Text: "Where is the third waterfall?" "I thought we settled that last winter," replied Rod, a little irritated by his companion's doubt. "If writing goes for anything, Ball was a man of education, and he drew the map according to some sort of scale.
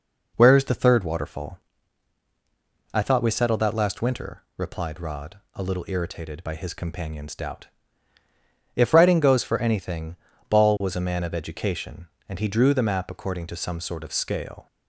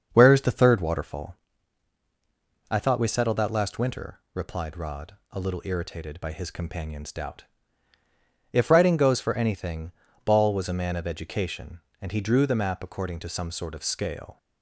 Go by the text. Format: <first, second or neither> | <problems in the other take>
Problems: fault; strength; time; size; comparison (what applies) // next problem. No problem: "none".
first | starts louder than the rest; until 1.1 s; 6.5 dB